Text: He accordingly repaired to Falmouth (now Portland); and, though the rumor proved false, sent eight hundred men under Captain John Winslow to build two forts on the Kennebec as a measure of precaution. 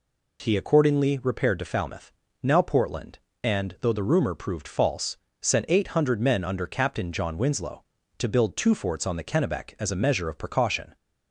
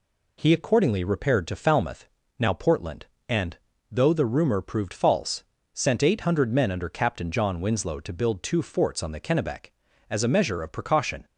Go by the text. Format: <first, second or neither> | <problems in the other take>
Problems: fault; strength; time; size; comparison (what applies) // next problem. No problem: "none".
neither | none